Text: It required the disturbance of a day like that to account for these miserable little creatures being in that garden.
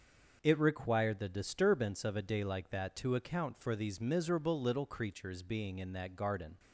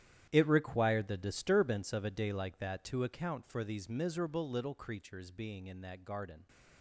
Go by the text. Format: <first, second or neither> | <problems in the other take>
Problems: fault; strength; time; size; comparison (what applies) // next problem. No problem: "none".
first | gets quieter; strong; throughout; 14.5 dB // starts louder than the rest; strong; until 1.3 s; 11 dB; also in the first